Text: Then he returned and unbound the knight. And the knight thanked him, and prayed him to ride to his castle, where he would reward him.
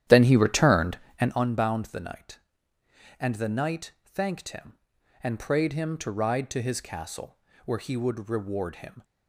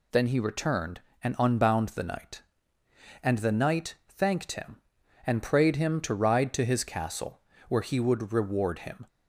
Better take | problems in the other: second | starts louder than the rest; strong; until 1.4 s; 11 dB

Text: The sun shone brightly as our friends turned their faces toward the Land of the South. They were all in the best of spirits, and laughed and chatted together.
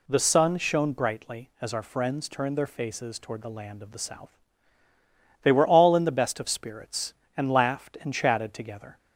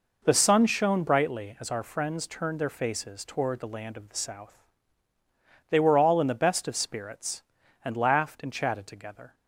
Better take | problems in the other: first | starts louder than the rest; noticeable; until 1.2 s; 5 dB

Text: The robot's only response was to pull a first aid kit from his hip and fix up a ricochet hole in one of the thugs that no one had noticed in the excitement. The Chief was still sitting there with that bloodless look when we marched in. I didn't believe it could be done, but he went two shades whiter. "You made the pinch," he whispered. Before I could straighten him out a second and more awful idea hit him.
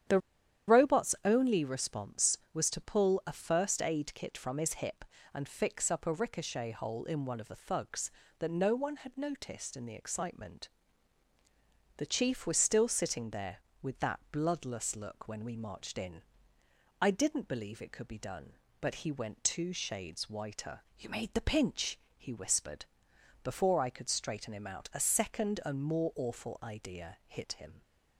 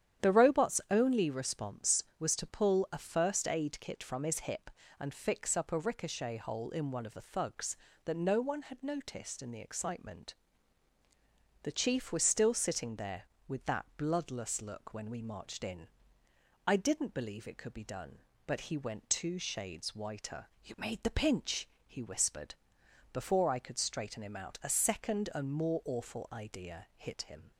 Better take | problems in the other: second | starts louder than the rest; strong; until 1.6 s; 10 dB; strong in the second // pauses between "The" and "robot's"; noticeable; at 0.1 s; 0.49 s long

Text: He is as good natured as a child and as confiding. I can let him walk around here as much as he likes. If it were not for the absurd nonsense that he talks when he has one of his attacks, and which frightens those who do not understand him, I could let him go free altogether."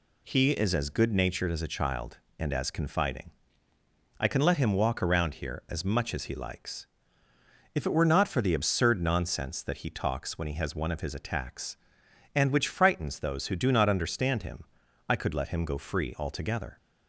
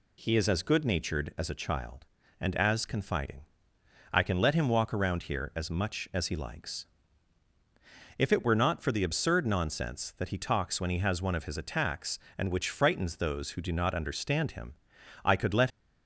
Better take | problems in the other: first | stops before "him go free altogether"; at 15.6 s

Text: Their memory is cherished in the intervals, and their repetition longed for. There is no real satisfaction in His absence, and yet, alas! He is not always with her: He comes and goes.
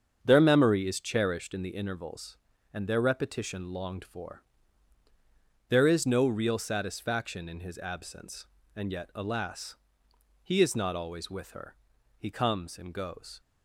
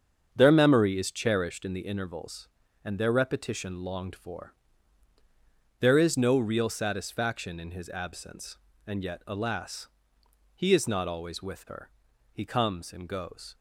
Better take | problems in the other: neither | starts louder than the rest; strong; the same in both

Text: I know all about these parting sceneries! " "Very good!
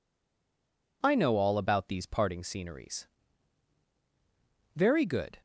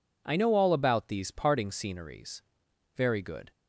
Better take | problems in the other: second | stays silent before the first word; until 1.0 s; 1.0 s long

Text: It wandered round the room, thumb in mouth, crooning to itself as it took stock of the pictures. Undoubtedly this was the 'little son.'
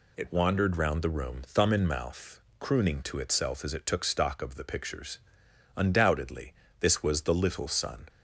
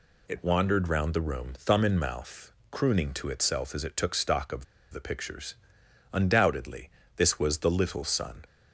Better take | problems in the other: first | pauses between "of" and "the"; slight; at 4.6 s; 0.26 s long // pauses between "Undoubtedly" and "this"; slight; at 6.8 s; 0.26 s long; slight in the first

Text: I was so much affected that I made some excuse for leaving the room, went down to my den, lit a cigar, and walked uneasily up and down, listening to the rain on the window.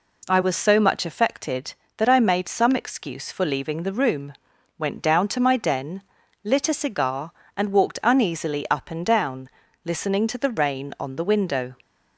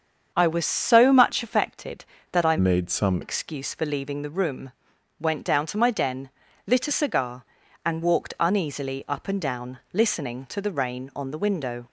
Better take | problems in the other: first | starts louder than the rest; until 1.3 s; 7 dB // changes voice from "made" to "some"; from 2.5 to 3.2 s; 0.7 s long

